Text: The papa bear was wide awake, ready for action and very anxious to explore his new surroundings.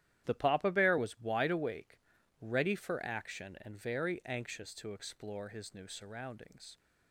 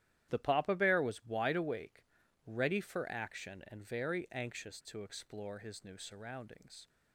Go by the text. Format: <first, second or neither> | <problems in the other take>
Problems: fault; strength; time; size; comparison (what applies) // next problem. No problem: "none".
neither | starts louder than the rest; strong; the same in both